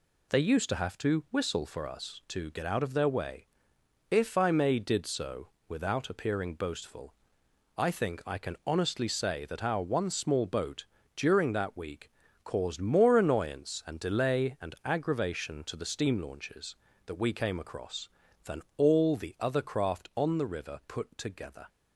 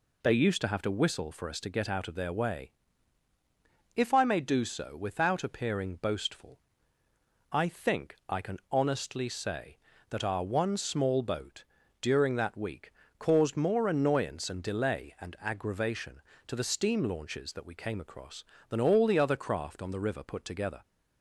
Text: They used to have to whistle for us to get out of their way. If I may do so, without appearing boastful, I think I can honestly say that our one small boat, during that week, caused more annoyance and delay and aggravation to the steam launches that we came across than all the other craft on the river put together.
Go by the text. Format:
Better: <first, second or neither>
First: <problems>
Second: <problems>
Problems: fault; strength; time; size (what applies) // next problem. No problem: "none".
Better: second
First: says "did" for "do"; at 4.7 s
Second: none